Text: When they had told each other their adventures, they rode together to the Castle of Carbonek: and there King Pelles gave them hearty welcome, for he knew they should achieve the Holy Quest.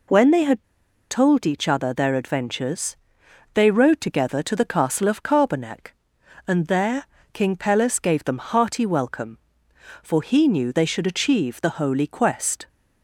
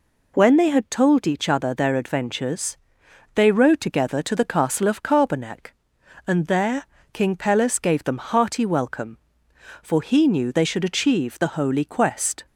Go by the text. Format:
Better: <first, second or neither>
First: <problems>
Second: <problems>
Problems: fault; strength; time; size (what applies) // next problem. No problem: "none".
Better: second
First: pauses between "had" and "told"; at 0.6 s; 0.45 s long // pauses between "there" and "King"; slight; at 7.0 s; 0.26 s long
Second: pauses between "there" and "King"; slight; at 6.8 s; 0.26 s long